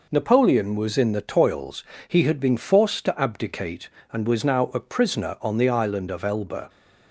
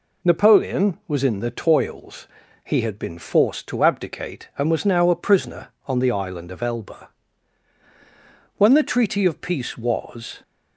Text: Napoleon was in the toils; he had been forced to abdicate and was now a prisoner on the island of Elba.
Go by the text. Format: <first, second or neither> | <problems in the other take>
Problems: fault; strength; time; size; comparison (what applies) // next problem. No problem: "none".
first | goes on to say "When the treaty of peace was"; strong; from 8.5 s on; 1.8 s long